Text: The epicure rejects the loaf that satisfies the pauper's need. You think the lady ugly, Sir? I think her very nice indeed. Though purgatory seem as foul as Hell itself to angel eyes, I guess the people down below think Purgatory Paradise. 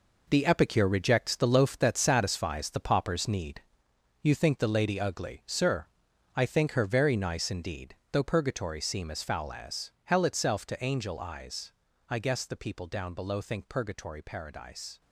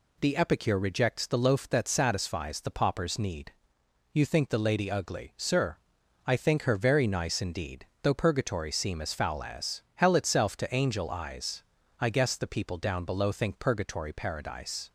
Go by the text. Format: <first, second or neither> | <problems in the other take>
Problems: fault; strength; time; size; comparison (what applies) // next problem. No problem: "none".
second | gets quieter; strong; throughout; 10 dB